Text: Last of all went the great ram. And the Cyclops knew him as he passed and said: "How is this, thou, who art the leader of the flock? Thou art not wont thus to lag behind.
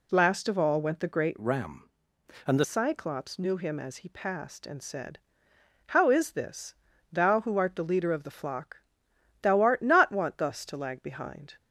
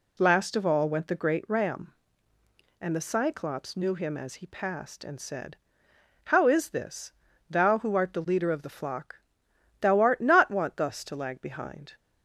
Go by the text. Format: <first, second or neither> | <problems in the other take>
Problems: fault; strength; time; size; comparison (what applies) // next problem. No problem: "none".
second | changes voice from "ram" to "the"; from 1.3 to 2.6 s; 1.3 s long